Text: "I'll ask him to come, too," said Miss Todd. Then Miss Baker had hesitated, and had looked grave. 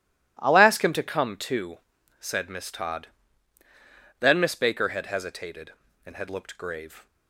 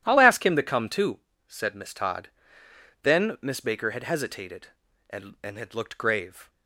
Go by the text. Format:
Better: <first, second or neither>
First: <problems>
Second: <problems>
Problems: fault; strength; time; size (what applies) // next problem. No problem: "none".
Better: first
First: none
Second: says "and" twice; at 5.4 s